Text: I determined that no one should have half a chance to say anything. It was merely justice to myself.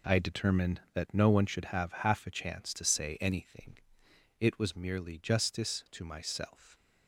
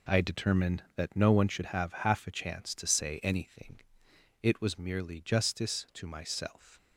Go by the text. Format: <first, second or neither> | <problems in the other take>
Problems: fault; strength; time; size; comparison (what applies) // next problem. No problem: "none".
neither | none